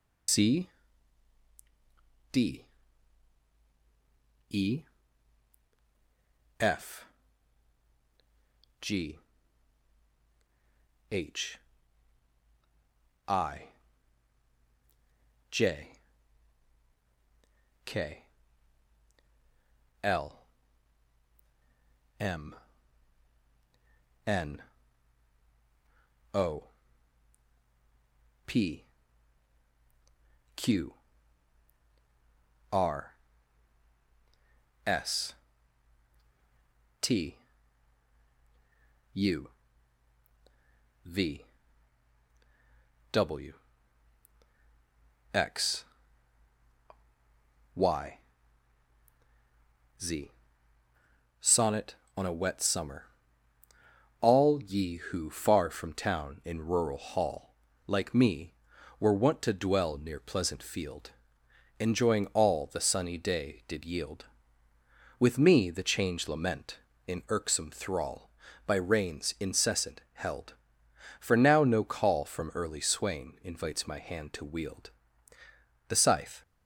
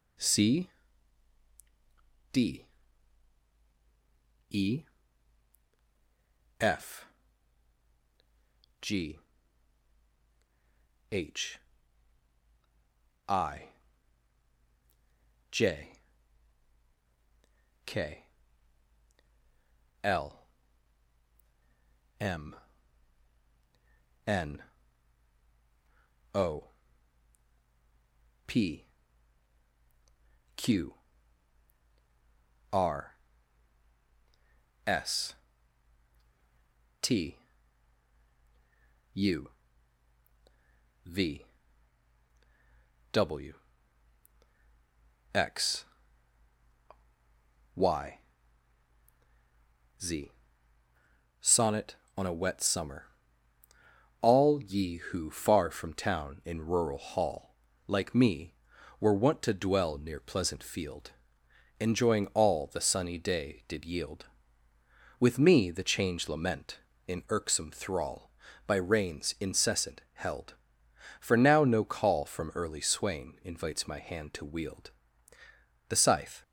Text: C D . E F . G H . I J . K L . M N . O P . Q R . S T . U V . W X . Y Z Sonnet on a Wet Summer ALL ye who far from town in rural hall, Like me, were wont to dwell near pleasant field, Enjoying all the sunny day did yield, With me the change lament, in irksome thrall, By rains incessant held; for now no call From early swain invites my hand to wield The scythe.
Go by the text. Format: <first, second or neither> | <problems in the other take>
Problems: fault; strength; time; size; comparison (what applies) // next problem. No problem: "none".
second | loses the start of "C"; at 0.2 s; 105 ms // pauses between "C" and "D"; strong; at 0.6 s; 1.6 s long; strong in the second // pauses between "E" and "F"; strong; at 4.8 s; 1.7 s long; strong in the second // pauses between "G" and "H"; strong; at 9.1 s; 1.9 s long; strong in the second // pauses between "I" and "J"; strong; at 13.6 s; 1.8 s long; strong in the second // pauses between "K" and "L"; strong; at 18.2 s; 1.8 s long; strong in the second // pauses between "M" and "N"; strong; at 22.5 s; 1.7 s long; strong in the second // pauses between "O" and "P"; strong; at 26.6 s; 1.8 s long; strong in the second // pauses between "Q" and "R"; strong; at 30.9 s; 1.7 s long; strong in the second // pauses between "S" and "T"; strong; at 35.3 s; 1.6 s long; strong in the second // pauses between "U" and "V"; strong; at 39.4 s; 1.5 s long; strong in the second // pauses between "W" and "X"; strong; at 43.5 s; 1.8 s long; strong in the second // pauses between "Y" and "Z"; strong; at 48.1 s; 1.8 s long; strong in the second // pauses between "Z" and "Sonnet"; at 50.3 s; 1.0 s long; also in the second // pauses between "Summer" and "ALL"; at 53.0 s; 1.1 s long; also in the second // pauses between "wield" and "The"; at 74.8 s; 1.0 s long; also in the second